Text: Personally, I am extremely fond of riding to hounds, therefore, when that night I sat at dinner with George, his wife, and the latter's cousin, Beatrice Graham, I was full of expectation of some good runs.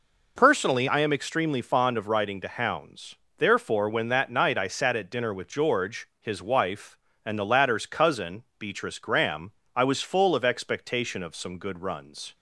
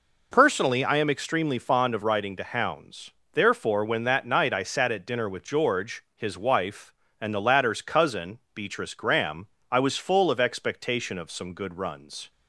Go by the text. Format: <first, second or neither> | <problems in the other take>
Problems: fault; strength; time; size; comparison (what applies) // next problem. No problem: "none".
neither | none